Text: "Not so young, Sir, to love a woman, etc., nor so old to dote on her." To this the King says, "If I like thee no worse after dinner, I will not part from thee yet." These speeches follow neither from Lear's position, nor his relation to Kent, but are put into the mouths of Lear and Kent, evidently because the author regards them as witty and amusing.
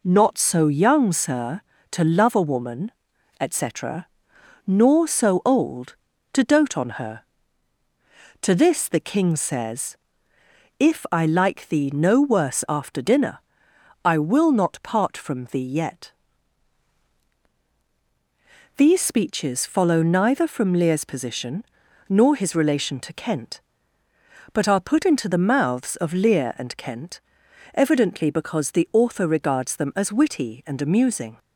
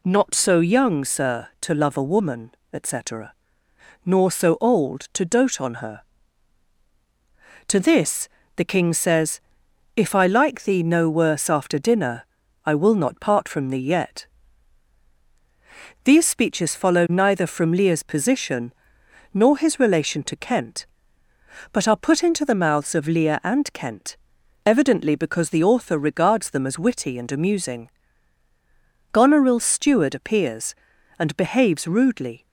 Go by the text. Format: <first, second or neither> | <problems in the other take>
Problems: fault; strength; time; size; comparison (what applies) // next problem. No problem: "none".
first | pauses between "this" and "the"; slight; at 8.2 s; 0.28 s long // goes on to say "Goneril's steward appears and behaves rudely"; strong; from 29.1 s on; 3.3 s long